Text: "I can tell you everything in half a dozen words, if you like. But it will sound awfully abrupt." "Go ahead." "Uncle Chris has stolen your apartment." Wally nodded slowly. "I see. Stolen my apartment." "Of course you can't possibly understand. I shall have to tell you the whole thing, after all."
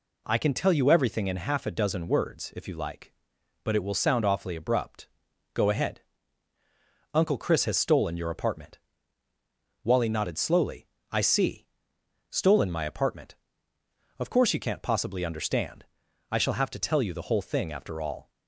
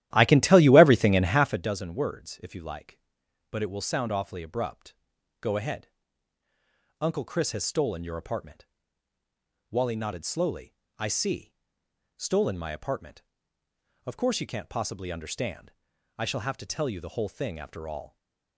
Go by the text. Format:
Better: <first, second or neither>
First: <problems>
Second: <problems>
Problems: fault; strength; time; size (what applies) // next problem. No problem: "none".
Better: first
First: none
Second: starts louder than the rest; strong; until 1.7 s; 13.5 dB // stays silent after the last word; slight; from 18.0 s on; 0.5 s long